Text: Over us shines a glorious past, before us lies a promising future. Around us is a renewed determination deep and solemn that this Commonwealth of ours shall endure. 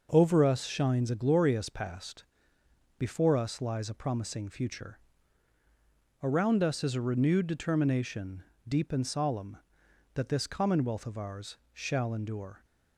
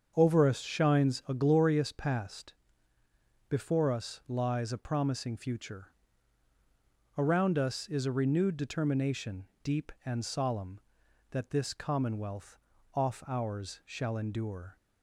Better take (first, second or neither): first